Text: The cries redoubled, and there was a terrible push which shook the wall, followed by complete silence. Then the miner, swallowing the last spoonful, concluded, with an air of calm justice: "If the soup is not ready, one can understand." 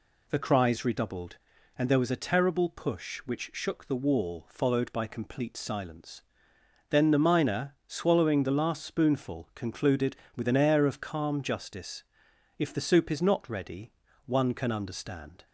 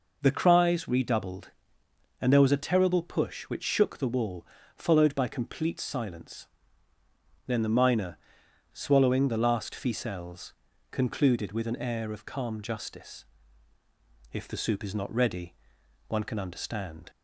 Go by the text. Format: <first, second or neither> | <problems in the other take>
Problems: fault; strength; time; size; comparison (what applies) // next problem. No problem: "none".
first | says "ficelles" for "spoonful"; at 9.7 s